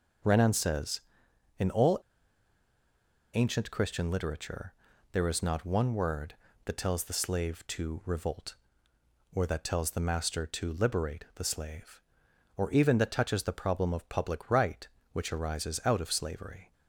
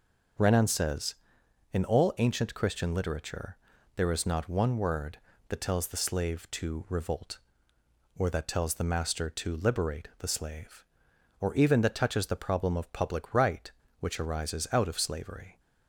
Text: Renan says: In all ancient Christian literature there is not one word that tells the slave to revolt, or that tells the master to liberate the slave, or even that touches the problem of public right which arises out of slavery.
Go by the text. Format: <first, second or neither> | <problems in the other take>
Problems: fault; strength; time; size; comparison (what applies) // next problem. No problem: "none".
second | pauses between "all" and "ancient"; strong; at 1.9 s; 1.3 s long // pauses between "literature" and "there"; at 4.7 s; 0.38 s long; also in the second